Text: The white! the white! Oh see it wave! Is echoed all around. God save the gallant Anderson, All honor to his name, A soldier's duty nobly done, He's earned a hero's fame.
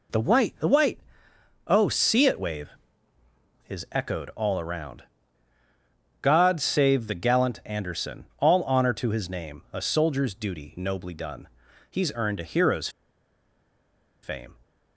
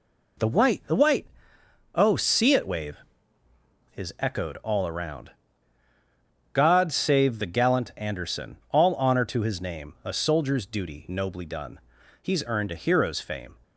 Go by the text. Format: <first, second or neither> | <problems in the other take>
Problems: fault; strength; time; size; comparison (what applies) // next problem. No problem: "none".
second | pauses between "hero's" and "fame"; strong; at 12.8 s; 1.3 s long